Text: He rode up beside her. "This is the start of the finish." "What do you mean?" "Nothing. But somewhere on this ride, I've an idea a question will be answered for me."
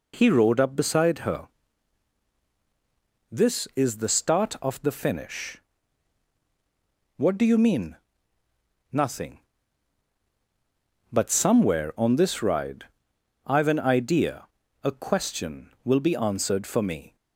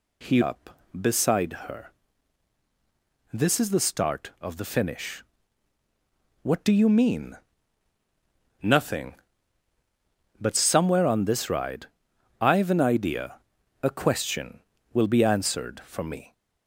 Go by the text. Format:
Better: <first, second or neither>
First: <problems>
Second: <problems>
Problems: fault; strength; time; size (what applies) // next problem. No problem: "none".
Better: first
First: pauses between "idea" and "a"; at 14.4 s; 0.38 s long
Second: skips "rode"; at 0.4 s // pauses between "idea" and "a"; at 13.3 s; 0.44 s long